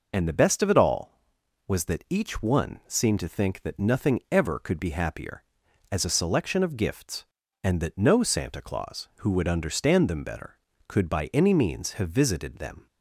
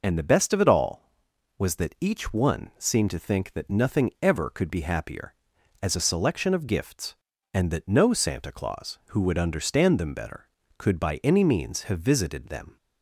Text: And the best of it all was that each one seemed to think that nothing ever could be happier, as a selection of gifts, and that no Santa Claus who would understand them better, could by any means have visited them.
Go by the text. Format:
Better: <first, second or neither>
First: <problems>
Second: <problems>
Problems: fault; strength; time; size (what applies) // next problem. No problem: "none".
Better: neither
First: none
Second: none